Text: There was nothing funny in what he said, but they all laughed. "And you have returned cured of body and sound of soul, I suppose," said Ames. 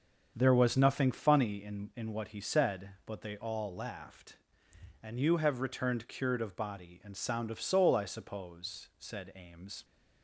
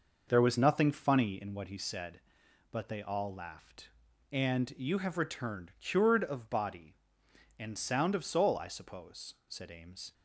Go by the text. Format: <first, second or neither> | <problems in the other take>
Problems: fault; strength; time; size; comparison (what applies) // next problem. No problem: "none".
second | starts louder than the rest; until 1.3 s; 7 dB // says "in" twice; at 1.9 s